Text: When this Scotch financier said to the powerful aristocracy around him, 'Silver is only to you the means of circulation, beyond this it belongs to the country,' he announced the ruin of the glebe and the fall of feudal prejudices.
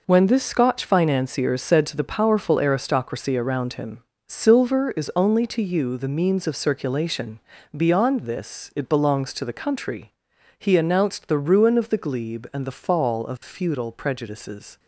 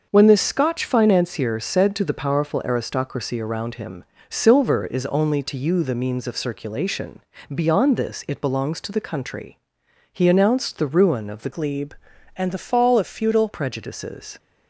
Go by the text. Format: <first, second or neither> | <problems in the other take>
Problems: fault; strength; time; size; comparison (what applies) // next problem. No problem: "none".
first | starts louder than the rest; until 1.1 s; 6.5 dB // changes voice from "glebe" to "feudal"; from 11.4 to 13.4 s; 2.0 s long